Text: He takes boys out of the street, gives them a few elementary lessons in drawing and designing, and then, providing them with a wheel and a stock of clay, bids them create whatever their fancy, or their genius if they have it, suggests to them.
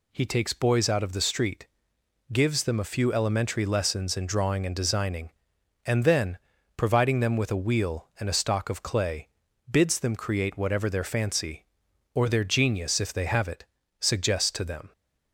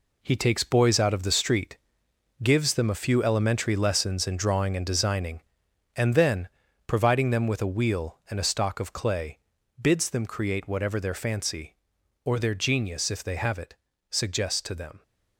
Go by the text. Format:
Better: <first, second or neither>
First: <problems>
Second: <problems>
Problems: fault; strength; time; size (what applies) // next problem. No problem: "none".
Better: first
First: none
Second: gets quieter; strong; throughout; 8 dB